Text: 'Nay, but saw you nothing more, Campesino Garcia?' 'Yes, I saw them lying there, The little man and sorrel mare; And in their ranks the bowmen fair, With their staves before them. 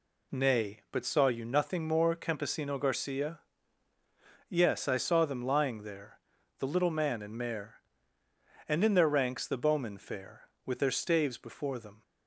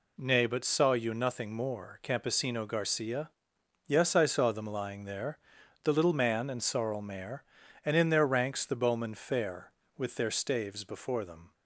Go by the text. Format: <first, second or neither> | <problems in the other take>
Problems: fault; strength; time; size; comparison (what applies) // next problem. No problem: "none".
second | skips "sorrel"; at 7.3 s